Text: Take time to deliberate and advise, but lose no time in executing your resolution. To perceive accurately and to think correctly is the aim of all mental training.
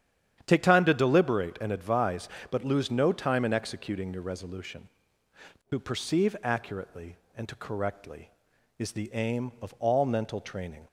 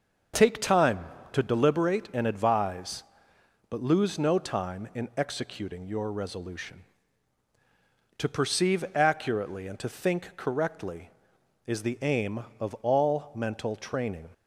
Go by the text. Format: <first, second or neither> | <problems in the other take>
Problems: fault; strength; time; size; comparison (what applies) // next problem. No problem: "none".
second | starts louder than the rest; strong; until 1.4 s; 9.5 dB; noticeable in the second // skips "think"; at 7.5 s